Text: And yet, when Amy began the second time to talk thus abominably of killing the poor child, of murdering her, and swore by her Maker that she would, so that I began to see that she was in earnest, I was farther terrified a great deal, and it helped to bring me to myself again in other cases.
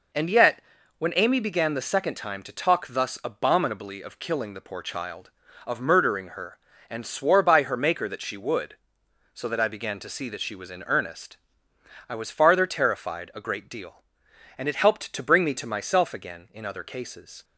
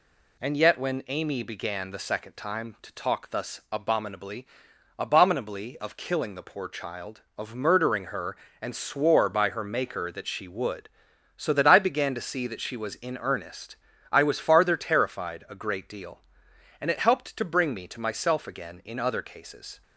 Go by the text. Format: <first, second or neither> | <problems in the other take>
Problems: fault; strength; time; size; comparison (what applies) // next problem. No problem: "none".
first | says "abominably" twice; at 4.9 s